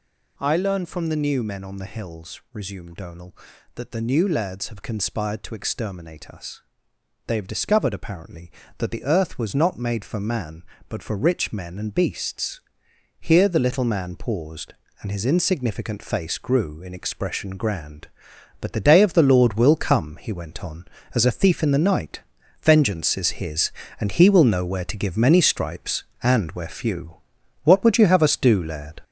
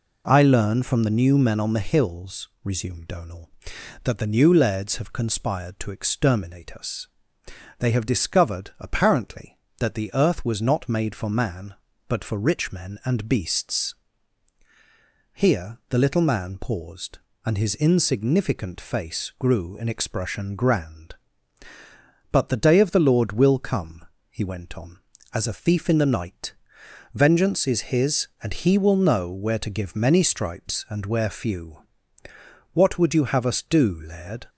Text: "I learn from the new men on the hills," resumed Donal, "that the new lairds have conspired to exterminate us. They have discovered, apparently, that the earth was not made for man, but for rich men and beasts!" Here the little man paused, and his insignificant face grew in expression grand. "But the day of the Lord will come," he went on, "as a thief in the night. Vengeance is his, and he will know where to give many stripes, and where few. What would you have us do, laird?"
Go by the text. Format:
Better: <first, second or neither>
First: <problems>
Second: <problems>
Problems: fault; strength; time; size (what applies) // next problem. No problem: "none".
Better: second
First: gets louder; throughout; 6.5 dB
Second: none